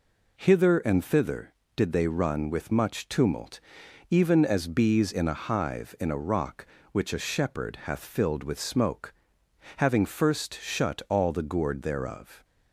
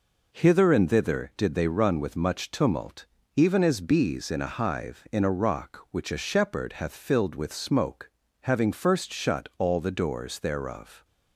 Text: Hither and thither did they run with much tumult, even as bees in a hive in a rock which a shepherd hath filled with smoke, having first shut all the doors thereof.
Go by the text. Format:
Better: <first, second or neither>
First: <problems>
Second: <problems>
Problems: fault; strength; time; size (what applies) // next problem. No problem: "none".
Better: second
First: says "gourd" for "doors"; at 11.4 s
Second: none